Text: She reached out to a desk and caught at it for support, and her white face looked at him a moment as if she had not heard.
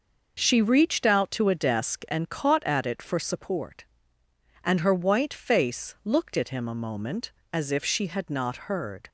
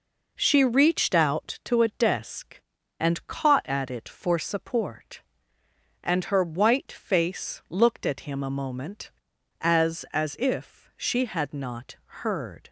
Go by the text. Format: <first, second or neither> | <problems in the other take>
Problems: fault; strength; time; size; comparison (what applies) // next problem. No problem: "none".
first | says "as" twice; at 10.1 s